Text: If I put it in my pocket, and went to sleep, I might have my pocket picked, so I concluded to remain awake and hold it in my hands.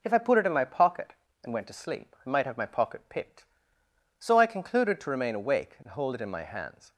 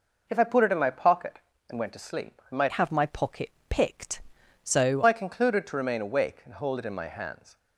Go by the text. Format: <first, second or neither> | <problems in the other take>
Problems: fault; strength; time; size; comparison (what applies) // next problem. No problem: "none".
first | changes voice from "have" to "so"; from 2.7 to 5.0 s; 2.3 s long // pauses between "pocket" and "picked"; slight; at 3.4 s; 0.20 s long